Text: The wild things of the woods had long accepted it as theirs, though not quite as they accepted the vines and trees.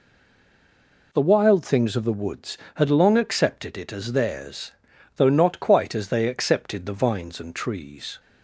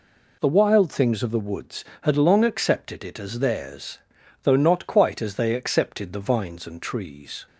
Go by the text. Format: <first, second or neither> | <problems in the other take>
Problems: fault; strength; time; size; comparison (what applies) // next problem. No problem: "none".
second | stays silent before the first word; until 1.1 s; 1.1 s long